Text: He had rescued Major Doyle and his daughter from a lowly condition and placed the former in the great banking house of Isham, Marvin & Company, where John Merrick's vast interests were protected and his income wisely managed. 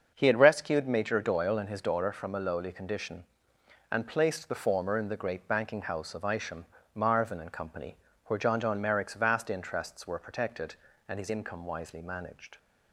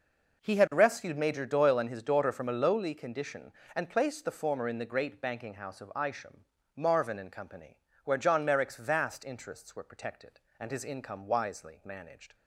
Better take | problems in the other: second | starts louder than the rest; until 1.1 s; 6.5 dB // says "John" twice; at 8.5 s

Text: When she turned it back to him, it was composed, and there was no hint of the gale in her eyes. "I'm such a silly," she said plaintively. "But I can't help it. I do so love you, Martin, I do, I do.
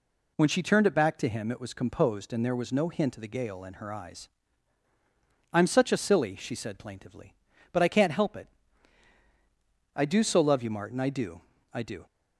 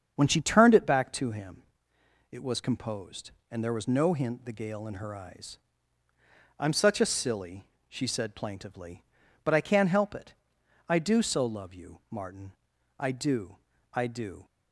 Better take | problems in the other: first | starts louder than the rest; strong; until 1.1 s; 7.5 dB // skips "of"; at 4.4 s

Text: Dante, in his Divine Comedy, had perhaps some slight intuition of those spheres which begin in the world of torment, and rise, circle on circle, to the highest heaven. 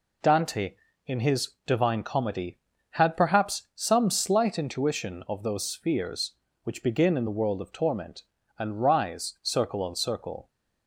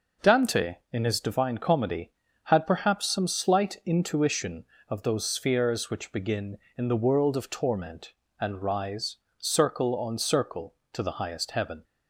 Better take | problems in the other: second | pauses between "his" and "Divine"; slight; at 1.5 s; 0.16 s long // stops before "to the highest heaven"; at 10.4 s

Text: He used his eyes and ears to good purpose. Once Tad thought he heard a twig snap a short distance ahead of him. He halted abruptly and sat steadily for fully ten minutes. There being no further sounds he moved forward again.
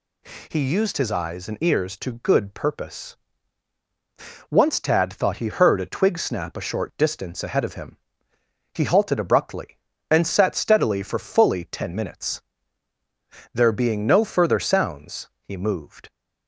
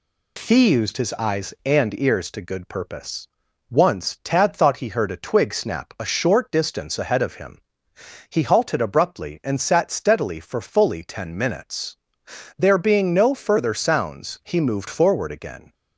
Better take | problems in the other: second | stops before "forward again"; at 16.0 s

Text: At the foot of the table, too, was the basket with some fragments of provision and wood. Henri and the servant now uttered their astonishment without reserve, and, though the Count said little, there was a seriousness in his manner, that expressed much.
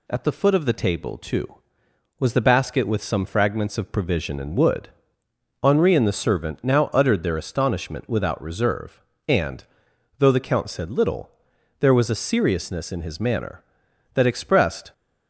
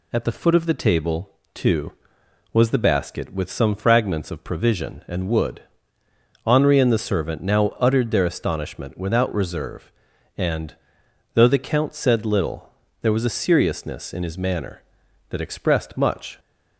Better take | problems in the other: second | stops before "much"; at 14.9 s

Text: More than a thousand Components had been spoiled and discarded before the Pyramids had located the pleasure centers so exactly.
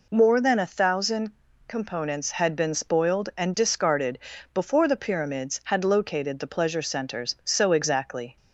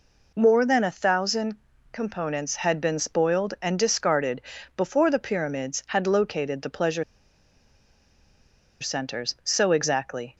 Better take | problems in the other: first | pauses between "thousand" and "Components"; slight; at 1.5 s; 0.36 s long; slight in the first // pauses between "discarded" and "before"; slight; at 4.4 s; 0.36 s long; slight in the first // pauses between "pleasure" and "centers"; strong; at 7.0 s; 1.7 s long

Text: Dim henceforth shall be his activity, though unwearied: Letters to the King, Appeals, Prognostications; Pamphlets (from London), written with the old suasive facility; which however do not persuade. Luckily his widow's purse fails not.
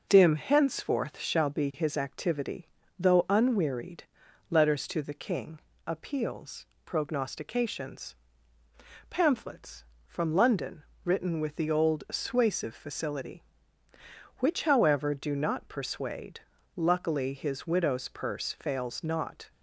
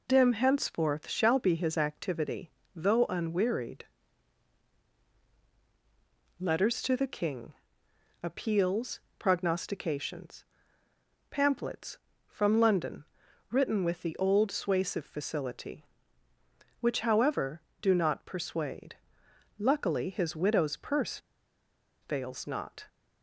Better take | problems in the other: first | pauses between "purse" and "fails"; noticeable; at 21.1 s; 0.83 s long

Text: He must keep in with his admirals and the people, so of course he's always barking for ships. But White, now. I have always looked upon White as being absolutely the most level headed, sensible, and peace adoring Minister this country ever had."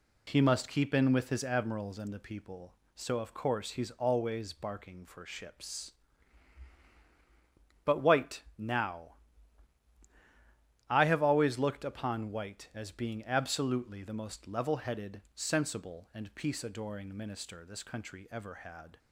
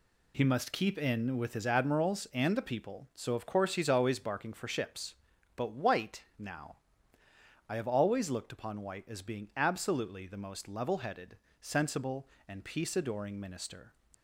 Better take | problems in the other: first | stops before "this country ever had"; at 14.1 s

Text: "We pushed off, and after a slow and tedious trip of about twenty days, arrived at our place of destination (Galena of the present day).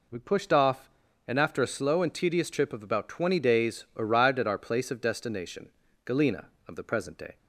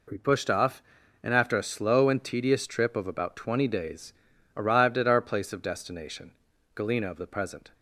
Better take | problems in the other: first | stops before "day"; at 7.7 s

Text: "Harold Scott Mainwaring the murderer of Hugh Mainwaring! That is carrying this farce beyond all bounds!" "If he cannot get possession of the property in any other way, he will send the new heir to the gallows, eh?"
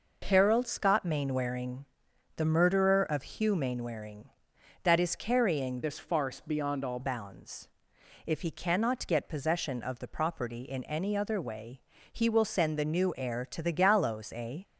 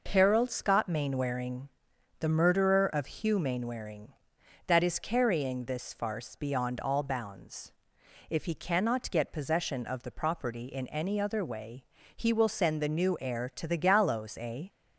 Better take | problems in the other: second | pauses between "Mainwaring" and "the"; noticeable; at 1.8 s; 0.54 s long; noticeable in the second // changes voice from "this" to "all"; from 5.8 to 6.9 s; 1.1 s long

